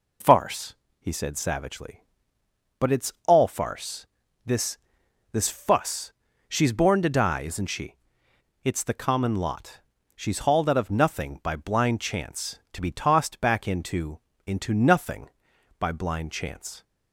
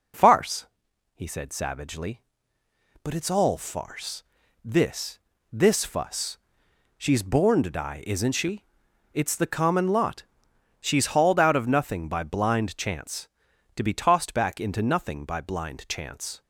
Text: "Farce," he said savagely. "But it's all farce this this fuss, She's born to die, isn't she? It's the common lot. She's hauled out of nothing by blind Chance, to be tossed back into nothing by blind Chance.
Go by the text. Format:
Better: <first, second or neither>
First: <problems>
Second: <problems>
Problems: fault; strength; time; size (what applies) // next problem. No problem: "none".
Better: second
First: pauses between "farce" and "this"; at 4.0 s; 0.40 s long // pauses between "this" and "this"; noticeable; at 4.7 s; 0.54 s long // says "into" twice; at 14.4 s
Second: pauses between "farce" and "this"; at 4.2 s; 0.40 s long // pauses between "this" and "this"; slight; at 5.1 s; 0.32 s long